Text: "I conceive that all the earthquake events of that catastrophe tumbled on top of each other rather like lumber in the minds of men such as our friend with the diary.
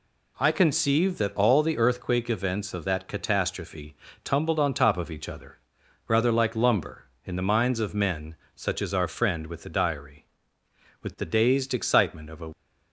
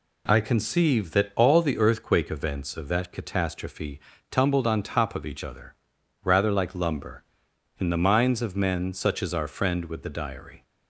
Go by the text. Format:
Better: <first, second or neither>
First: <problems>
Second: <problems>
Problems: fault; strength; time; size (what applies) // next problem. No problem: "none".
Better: second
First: pauses between "catastrophe" and "tumbled"; slight; at 3.9 s; 0.30 s long // pauses between "other" and "rather"; noticeable; at 5.5 s; 0.50 s long // pauses between "men" and "such"; slight; at 8.3 s; 0.20 s long // goes on to say "With the dazed excitement of a"; from 11.0 s on; 1.4 s long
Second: pauses between "catastrophe" and "tumbled"; slight; at 4.0 s; 0.28 s long // pauses between "other" and "rather"; noticeable; at 5.7 s; 0.48 s long